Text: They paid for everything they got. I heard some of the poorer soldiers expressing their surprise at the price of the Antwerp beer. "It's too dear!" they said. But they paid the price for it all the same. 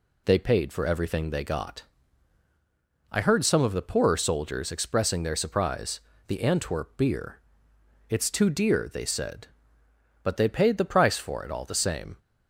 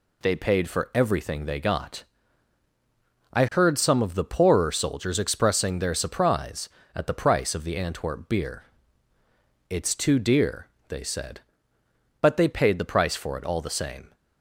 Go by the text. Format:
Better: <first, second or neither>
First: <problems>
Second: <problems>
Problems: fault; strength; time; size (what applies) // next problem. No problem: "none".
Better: second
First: skips "at the price of"; at 6.1 s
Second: none